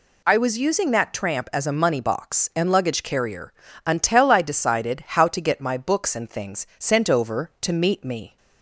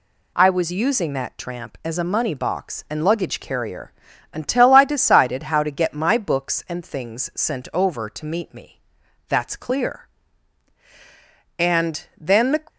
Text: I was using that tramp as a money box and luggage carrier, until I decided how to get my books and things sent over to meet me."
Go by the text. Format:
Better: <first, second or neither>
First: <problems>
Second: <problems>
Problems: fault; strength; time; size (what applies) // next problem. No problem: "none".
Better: first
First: none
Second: goes on to say "That's clear And then the"; strong; from 9.2 s on; 3.3 s long